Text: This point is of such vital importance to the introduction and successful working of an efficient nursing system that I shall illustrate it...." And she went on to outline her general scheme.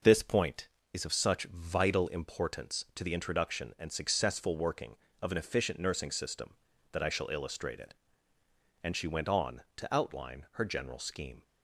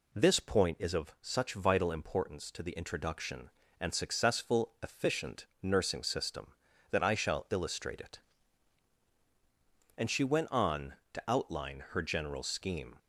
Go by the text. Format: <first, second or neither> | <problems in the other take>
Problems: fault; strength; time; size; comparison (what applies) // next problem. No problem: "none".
first | skips "working of an"; at 4.7 s // pauses between "efficient" and "nursing"; slight; at 5.4 s; 0.16 s long